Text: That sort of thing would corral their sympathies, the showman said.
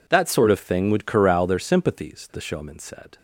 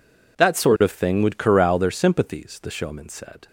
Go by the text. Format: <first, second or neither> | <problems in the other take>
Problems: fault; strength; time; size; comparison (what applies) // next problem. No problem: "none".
neither | none